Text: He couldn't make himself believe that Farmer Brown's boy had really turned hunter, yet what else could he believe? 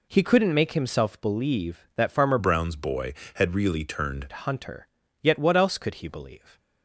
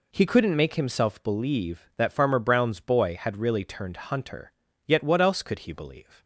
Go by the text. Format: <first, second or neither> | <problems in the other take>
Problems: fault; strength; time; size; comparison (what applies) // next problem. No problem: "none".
second | changes voice from "Brown's" to "turned"; from 2.3 to 4.2 s; 1.9 s long